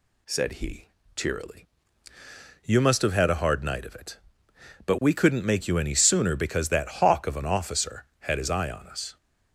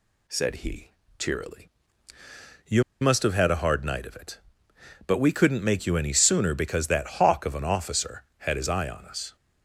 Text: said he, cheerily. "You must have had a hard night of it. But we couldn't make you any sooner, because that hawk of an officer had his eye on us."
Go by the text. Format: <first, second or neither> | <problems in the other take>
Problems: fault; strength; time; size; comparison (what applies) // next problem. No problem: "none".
first | pauses between "You" and "must"; slight; at 2.8 s; 0.18 s long